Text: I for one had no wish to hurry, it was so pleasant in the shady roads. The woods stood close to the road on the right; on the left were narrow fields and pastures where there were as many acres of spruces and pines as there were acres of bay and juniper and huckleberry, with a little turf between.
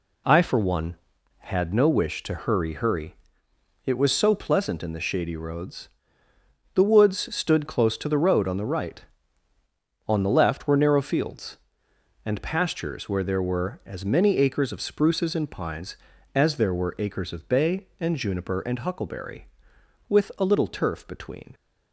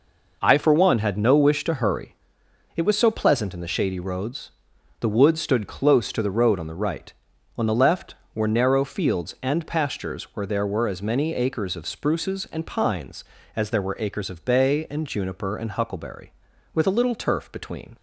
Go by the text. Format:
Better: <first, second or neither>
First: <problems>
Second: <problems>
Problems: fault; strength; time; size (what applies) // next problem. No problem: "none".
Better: second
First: says "hurry" twice; at 2.7 s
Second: none